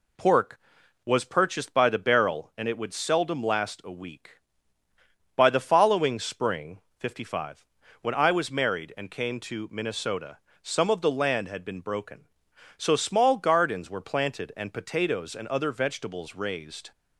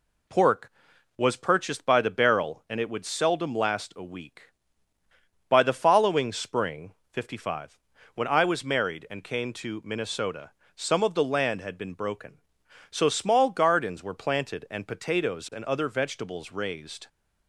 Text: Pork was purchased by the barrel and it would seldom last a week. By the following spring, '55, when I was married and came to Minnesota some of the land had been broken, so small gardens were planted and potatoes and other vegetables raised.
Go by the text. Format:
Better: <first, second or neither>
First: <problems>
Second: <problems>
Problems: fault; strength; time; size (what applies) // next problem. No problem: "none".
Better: neither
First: pauses between "Minnesota" and "some"; slight; at 10.3 s; 0.26 s long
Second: pauses between "Minnesota" and "some"; slight; at 10.5 s; 0.26 s long